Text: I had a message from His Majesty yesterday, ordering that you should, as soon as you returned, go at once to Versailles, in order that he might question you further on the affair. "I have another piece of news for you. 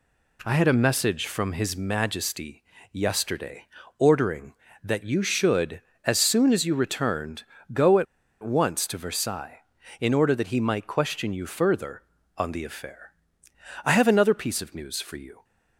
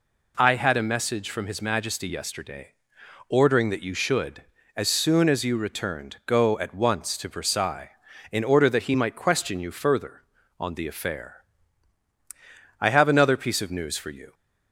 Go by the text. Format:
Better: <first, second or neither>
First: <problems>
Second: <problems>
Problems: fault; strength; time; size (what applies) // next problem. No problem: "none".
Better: second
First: pauses between "Majesty" and "yesterday"; slight; at 2.6 s; 0.30 s long // pauses between "at" and "once"; at 8.0 s; 0.38 s long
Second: none